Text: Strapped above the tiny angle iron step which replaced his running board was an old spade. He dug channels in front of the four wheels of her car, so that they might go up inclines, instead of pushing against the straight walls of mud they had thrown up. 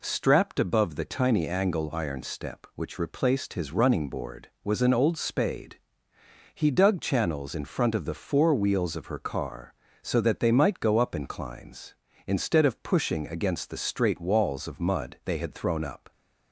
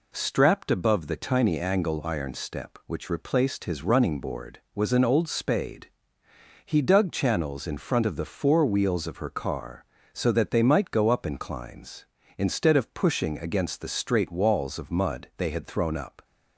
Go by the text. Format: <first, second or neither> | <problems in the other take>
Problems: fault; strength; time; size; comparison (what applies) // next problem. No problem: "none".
neither | none